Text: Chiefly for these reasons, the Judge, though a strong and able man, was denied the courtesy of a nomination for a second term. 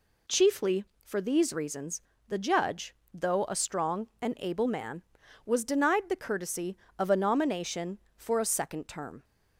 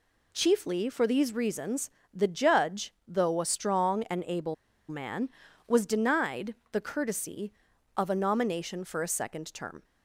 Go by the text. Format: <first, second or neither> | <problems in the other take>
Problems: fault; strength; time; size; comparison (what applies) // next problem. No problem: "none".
first | pauses between "able" and "man"; slight; at 4.5 s; 0.34 s long // pauses between "denied" and "the"; slight; at 6.5 s; 0.18 s long